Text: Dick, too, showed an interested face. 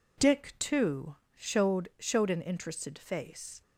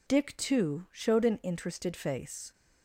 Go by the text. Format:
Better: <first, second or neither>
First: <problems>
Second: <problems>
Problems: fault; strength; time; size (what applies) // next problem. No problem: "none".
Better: second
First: says "showed" twice; at 1.9 s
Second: none